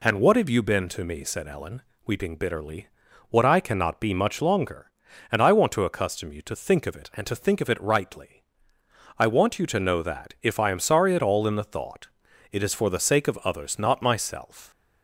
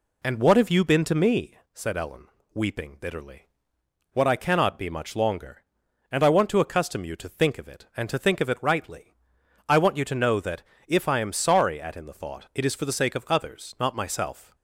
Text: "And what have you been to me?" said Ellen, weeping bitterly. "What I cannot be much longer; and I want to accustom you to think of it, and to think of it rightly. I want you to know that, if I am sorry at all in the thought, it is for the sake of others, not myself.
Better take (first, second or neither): first